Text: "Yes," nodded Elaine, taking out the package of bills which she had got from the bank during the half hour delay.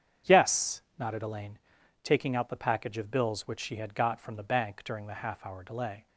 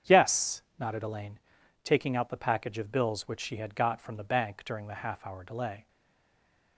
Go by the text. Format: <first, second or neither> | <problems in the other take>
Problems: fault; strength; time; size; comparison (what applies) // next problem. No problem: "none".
first | starts louder than the rest; strong; until 1.2 s; 8 dB; strong in the first // stays silent after the last word; slight; from 5.8 s on; 0.9 s long